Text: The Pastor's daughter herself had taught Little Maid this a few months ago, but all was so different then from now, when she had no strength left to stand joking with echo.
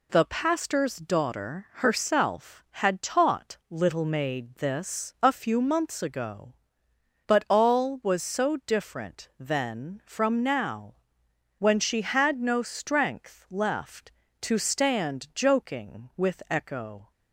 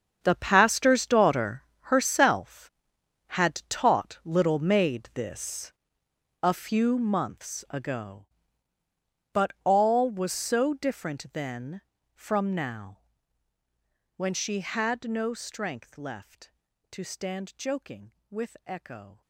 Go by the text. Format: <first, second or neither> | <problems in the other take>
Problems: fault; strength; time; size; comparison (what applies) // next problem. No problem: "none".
first | gets quieter; strong; throughout; 15 dB // pauses between "daughter" and "herself"; slight; at 1.6 s; 0.22 s long // pauses between "this" and "a"; noticeable; at 5.7 s; 0.72 s long